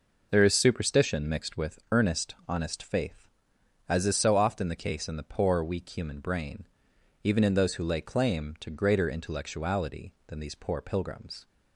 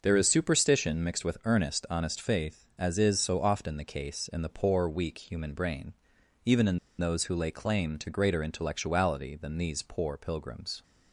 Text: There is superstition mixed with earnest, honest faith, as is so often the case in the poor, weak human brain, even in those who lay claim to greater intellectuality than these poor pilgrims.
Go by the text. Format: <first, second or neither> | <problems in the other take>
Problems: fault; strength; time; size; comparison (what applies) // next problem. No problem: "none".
first | pauses between "in" and "those"; slight; at 6.7 s; 0.20 s long